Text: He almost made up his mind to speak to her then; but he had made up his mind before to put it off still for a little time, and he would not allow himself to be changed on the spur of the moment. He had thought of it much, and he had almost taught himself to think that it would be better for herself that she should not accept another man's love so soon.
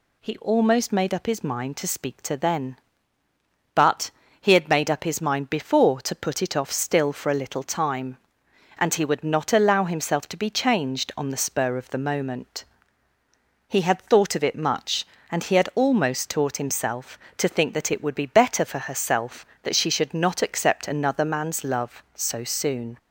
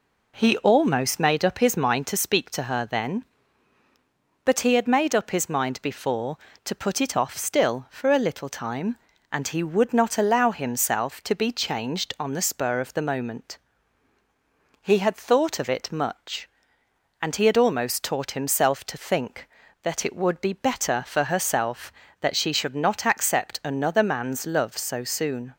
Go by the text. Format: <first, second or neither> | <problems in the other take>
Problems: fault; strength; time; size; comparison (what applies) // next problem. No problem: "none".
second | skips "her"; at 2.3 s // pauses between "but" and "he"; slight; at 4.1 s; 0.30 s long